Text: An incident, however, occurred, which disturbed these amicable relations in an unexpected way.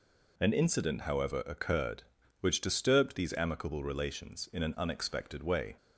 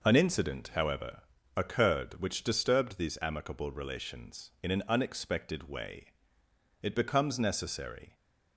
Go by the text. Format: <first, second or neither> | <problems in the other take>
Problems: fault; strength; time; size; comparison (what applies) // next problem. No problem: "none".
first | goes on to say "It becomes necessary"; from 6.8 s on; 1.3 s long